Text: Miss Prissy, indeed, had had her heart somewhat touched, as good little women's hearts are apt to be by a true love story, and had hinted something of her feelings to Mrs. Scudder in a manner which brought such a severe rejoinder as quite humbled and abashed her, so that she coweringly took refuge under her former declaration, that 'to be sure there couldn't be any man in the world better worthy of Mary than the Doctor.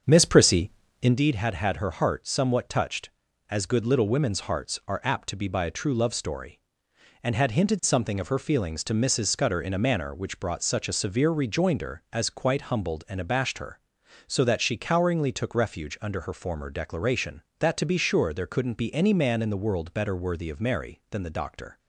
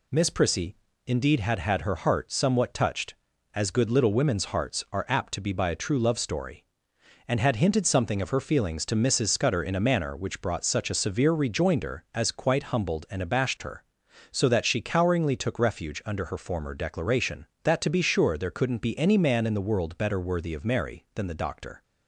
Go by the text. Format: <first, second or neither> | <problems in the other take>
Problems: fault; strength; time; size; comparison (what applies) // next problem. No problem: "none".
second | starts louder than the rest; until 1.2 s; 7 dB